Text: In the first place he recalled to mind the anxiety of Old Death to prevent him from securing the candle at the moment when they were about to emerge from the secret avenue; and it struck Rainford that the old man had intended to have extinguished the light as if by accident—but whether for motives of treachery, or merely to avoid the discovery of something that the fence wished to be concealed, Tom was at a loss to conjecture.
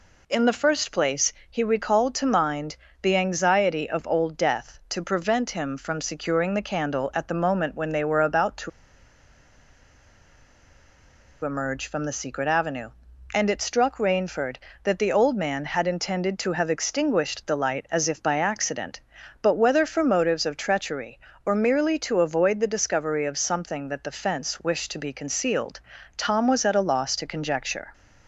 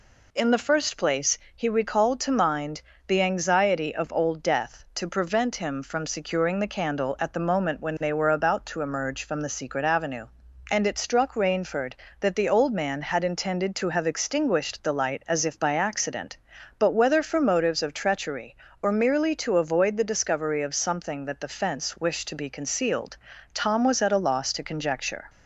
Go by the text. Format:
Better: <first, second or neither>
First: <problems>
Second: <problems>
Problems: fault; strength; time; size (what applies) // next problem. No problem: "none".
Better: second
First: pauses between "place" and "he"; slight; at 1.3 s; 0.20 s long // pauses between "mind" and "the"; slight; at 2.7 s; 0.28 s long // pauses between "to" and "emerge"; strong; at 8.6 s; 2.7 s long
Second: pauses between "place" and "he"; slight; at 1.3 s; 0.20 s long // pauses between "mind" and "the"; slight; at 2.8 s; 0.28 s long